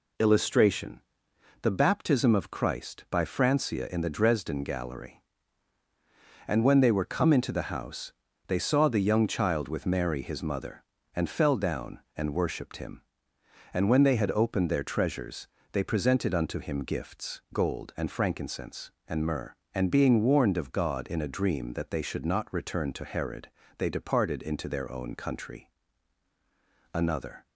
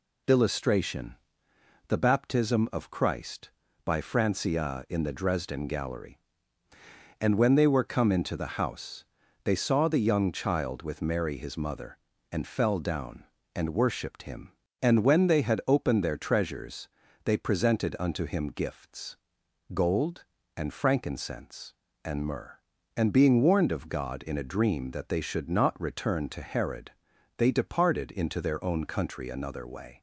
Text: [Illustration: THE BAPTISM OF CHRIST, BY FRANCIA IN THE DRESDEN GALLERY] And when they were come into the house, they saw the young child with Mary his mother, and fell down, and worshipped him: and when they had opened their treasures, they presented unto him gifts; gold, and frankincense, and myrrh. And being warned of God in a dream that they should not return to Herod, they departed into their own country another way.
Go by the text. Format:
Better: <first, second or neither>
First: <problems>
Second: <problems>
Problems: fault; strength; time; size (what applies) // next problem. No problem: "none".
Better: second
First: pauses between "country" and "another"; at 25.6 s; 1.2 s long // stops before "way"; at 27.4 s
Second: none